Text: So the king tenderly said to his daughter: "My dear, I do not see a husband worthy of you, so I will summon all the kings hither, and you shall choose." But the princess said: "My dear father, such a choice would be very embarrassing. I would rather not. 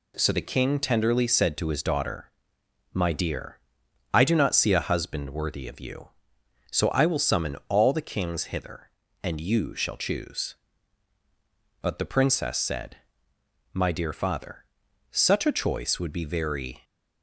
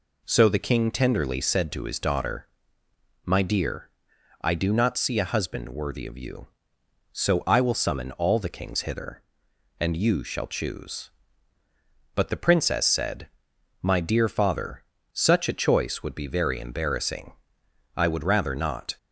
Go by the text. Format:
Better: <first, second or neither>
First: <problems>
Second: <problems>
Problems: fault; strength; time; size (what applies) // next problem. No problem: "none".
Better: second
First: stops before "embarrassing I would rather not"; at 16.8 s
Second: none